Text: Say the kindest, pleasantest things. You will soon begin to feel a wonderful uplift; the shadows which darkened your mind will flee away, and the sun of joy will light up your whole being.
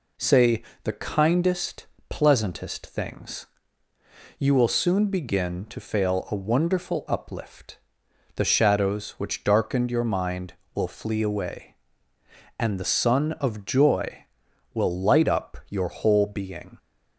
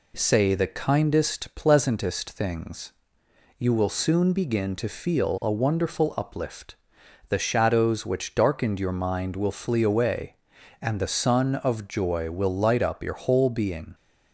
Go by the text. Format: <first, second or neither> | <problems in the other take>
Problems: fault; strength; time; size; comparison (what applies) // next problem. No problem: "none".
second | pauses between "Say" and "the"; slight; at 0.6 s; 0.22 s long // says "fail" for "feel"; at 5.7 s